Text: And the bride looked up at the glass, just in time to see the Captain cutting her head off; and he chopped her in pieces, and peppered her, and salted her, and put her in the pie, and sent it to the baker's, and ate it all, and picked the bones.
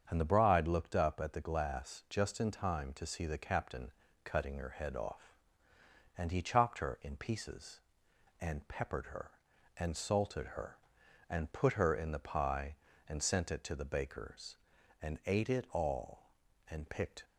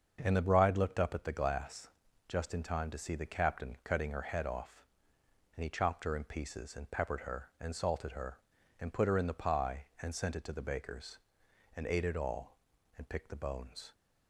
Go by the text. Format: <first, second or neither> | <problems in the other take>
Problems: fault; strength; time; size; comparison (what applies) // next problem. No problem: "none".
second | starts louder than the rest; strong; until 1.1 s; 7.5 dB; also in the second // pauses between "Captain" and "cutting"; slight; at 3.8 s; 0.34 s long // stops before "the bones"; at 17.2 s